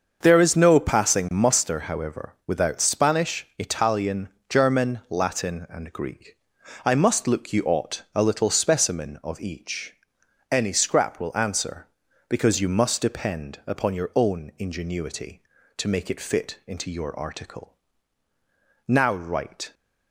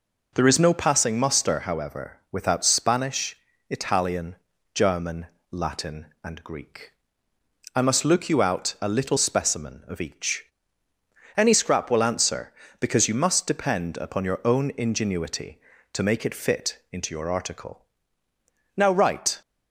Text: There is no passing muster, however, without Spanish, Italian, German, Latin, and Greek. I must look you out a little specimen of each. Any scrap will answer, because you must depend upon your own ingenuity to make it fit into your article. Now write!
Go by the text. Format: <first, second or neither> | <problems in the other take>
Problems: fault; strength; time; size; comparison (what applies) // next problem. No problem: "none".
second | starts louder than the rest; until 1.2 s; 6.5 dB // says "ought" for "out"; at 7.6 s